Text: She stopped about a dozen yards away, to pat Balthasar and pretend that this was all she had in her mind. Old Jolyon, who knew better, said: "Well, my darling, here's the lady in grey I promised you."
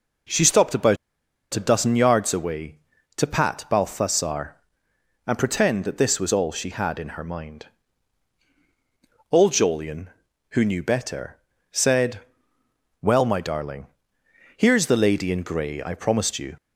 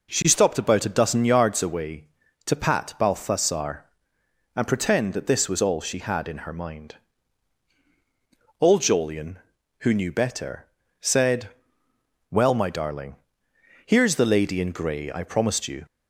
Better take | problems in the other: second | pauses between "about" and "a"; noticeable; at 0.9 s; 0.57 s long

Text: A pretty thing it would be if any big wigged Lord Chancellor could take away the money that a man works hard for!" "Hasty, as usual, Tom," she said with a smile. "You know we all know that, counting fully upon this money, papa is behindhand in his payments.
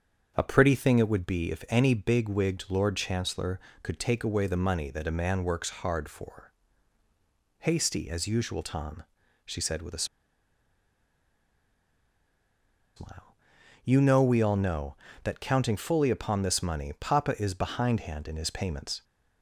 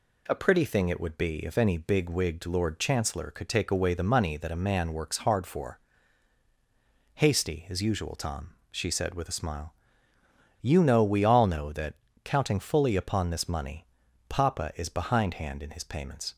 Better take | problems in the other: second | starts louder than the rest; strong; until 1.3 s; 7 dB // pauses between "a" and "smile"; strong; at 10.0 s; 2.9 s long

